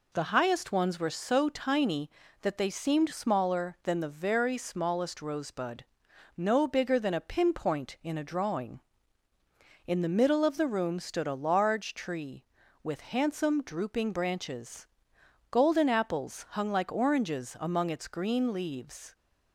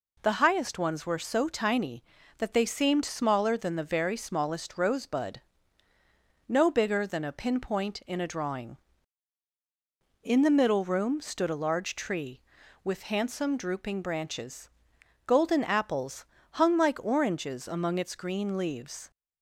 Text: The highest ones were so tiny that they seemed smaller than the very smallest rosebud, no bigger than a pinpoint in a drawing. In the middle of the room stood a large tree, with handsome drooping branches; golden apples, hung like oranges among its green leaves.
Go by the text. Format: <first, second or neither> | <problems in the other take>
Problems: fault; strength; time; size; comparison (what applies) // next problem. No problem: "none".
first | skips "of the"; at 10.8 s